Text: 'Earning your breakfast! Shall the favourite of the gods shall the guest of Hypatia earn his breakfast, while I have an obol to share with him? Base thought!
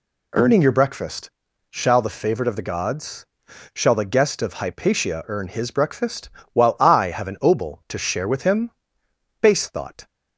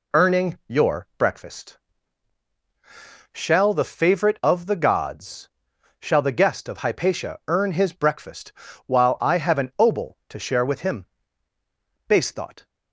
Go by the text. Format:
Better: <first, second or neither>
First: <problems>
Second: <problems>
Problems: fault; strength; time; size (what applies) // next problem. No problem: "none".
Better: neither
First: pauses between "gods" and "shall"; noticeable; at 3.2 s; 0.48 s long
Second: pauses between "gods" and "shall"; noticeable; at 5.4 s; 0.54 s long